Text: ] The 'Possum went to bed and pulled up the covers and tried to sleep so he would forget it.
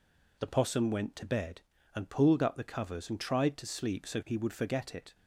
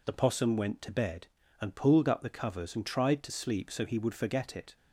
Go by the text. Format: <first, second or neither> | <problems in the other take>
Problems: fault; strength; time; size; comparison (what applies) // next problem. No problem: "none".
neither | none